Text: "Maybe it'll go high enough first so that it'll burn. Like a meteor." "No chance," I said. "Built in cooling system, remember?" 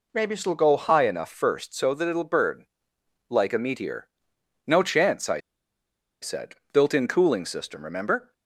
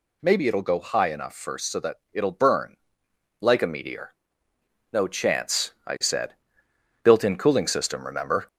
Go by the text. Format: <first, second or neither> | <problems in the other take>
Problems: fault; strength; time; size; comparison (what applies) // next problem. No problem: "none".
second | pauses between "I" and "said"; noticeable; at 5.3 s; 0.84 s long